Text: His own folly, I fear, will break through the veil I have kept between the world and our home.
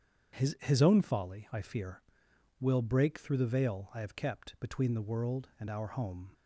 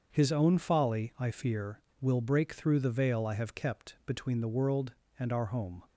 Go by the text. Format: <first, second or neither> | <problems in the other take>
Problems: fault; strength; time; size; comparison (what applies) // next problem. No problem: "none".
second | starts louder than the rest; strong; until 1.4 s; 8 dB; also in the second // says "His" twice; at 0.5 s